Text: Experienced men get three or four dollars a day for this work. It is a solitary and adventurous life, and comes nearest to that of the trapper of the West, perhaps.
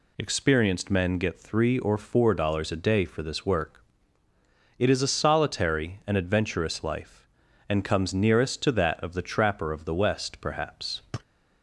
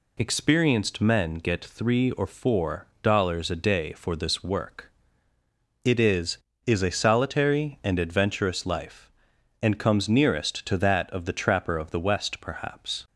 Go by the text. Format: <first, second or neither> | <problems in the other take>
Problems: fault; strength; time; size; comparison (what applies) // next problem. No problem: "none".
first | says "is" twice; at 6.6 s